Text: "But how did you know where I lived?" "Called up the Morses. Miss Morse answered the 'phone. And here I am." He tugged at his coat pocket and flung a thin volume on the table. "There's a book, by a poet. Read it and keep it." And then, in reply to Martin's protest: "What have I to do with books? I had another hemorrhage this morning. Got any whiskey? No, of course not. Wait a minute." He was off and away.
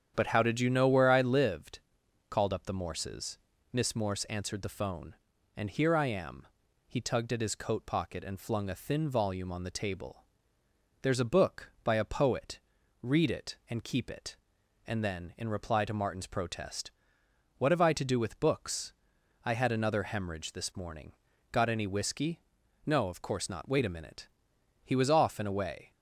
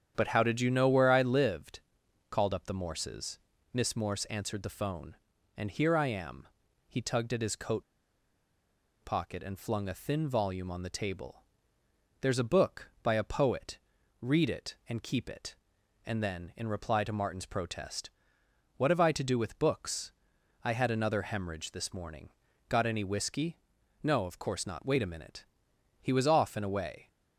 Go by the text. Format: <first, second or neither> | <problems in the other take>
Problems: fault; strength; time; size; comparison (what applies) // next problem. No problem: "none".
first | starts louder than the rest; strong; until 1.1 s; 8.5 dB; strong in the first // pauses between "coat" and "pocket"; at 7.8 s; 1.2 s long